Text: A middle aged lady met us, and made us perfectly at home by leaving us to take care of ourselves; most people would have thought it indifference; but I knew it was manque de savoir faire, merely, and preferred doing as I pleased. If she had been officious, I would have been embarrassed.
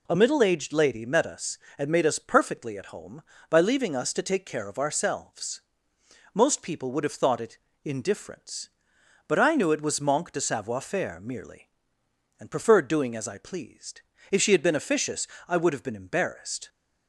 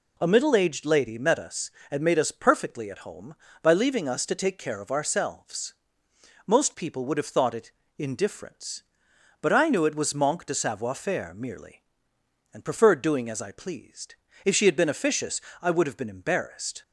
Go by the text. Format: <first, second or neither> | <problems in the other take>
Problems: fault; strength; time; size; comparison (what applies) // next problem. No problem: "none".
neither | pauses between "it" and "indifference"; slight; the same in both